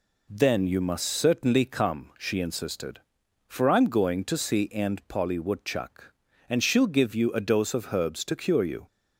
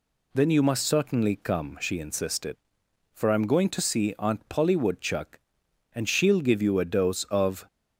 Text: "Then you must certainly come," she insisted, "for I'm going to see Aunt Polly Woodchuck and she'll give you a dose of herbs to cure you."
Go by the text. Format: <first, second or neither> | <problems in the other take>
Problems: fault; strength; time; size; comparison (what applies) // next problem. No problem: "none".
first | stops before "herbs to cure you"; at 7.6 s